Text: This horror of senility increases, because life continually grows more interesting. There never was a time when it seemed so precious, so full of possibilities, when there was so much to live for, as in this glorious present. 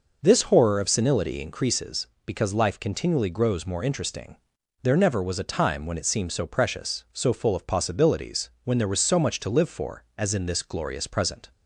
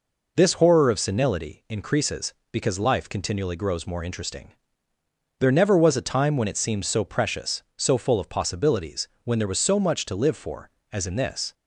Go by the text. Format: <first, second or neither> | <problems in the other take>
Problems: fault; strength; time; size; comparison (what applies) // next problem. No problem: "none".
first | stops before "glorious present"; at 11.5 s